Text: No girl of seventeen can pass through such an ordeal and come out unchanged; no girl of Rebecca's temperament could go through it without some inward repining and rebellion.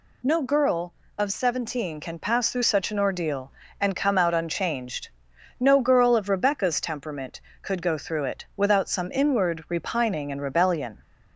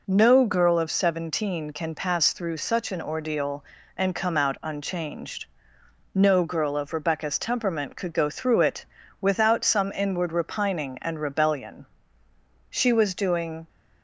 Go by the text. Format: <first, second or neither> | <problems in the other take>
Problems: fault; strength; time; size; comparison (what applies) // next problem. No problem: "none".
first | pauses between "it" and "without"; slight; at 8.8 s; 0.34 s long // goes on to say "She was doing"; noticeable; from 12.6 s on; 0.98 s long